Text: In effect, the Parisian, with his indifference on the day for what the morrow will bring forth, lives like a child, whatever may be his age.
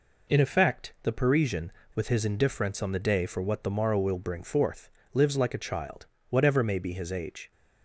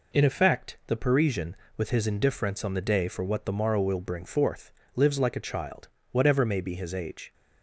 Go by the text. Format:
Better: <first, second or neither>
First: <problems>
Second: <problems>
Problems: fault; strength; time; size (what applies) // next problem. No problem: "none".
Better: neither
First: none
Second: none